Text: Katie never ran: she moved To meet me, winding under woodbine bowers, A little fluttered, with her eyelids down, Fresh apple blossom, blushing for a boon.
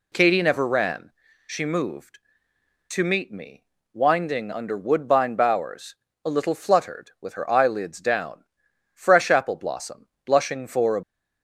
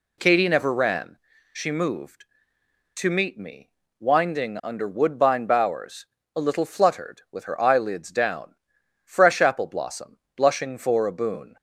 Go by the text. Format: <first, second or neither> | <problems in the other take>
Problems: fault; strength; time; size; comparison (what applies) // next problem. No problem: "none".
second | stops before "boon"; at 11.0 s